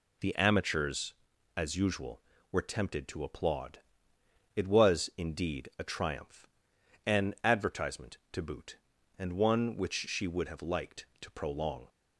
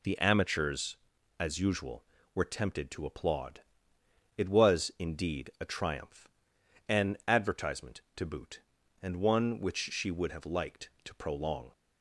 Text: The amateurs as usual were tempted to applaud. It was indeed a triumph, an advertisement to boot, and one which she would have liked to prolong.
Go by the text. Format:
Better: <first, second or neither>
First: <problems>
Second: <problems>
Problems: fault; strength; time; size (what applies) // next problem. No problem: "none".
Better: neither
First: none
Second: none